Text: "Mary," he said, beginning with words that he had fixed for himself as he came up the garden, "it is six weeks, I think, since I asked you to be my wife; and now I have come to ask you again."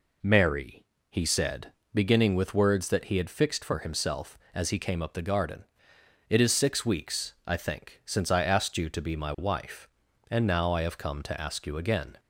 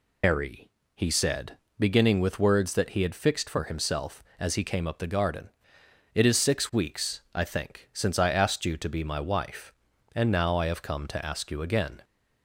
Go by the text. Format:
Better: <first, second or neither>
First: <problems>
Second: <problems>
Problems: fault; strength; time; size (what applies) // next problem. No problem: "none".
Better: first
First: none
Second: loses the start of "Mary"; at 0.2 s; 165 ms